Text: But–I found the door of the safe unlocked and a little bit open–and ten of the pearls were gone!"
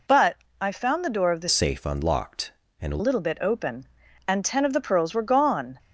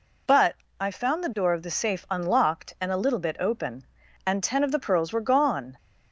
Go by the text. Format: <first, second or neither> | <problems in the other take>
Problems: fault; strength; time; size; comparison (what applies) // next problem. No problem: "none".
second | changes voice from "safe" to "a"; from 1.4 to 2.9 s; 1.5 s long